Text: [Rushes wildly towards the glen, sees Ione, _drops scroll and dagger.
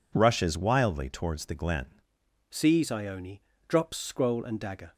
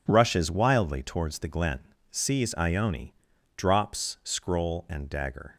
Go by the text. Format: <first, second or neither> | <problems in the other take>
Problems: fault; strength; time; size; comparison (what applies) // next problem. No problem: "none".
second | changes voice at "sees"; from 2.4 s on; 2.5 s long